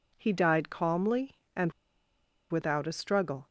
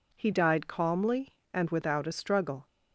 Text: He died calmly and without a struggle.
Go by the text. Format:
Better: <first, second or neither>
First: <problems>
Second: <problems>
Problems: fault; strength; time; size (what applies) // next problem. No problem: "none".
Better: second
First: pauses between "and" and "without"; noticeable; at 1.7 s; 0.78 s long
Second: none